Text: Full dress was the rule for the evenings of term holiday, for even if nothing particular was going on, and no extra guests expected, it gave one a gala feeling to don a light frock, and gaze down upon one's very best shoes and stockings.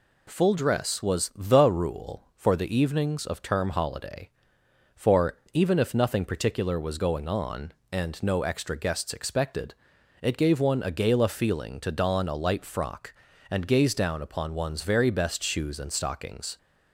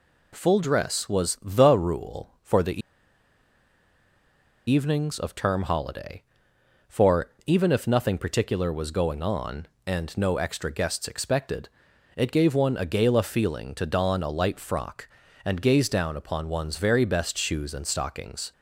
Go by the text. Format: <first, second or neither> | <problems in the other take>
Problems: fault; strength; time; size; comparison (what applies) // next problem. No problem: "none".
first | pauses between "the" and "evenings"; strong; at 2.8 s; 1.8 s long // pauses between "for" and "even"; slight; at 7.2 s; 0.16 s long; slight in the first